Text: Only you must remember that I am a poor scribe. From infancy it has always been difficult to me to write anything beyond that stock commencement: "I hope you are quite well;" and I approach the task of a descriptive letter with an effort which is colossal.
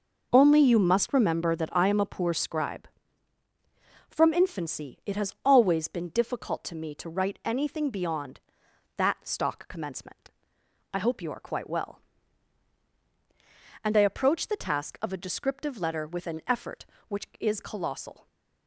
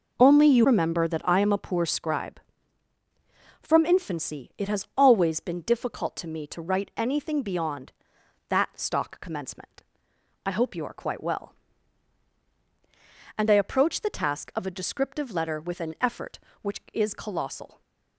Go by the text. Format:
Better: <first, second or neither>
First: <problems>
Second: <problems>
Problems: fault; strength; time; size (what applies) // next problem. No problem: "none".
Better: first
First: none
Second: skips "must"; at 0.6 s